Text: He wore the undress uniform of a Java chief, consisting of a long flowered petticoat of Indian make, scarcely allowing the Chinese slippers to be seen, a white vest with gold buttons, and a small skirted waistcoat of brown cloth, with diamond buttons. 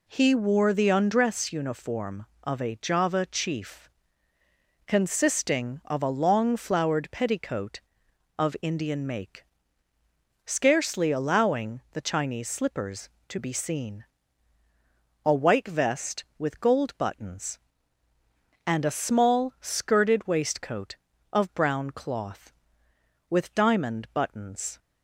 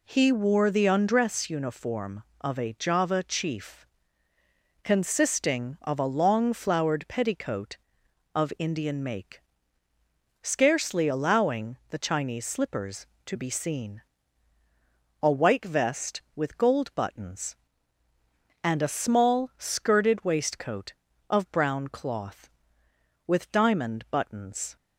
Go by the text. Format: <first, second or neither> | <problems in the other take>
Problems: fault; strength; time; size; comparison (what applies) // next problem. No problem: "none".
neither | none